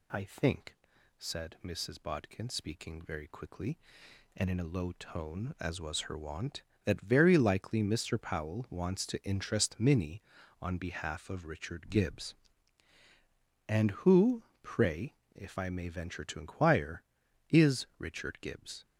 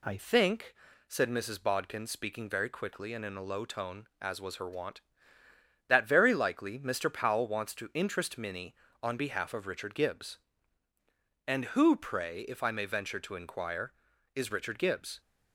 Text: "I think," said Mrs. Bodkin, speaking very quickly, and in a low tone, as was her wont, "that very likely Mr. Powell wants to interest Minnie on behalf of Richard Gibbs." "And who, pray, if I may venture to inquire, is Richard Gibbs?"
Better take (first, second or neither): first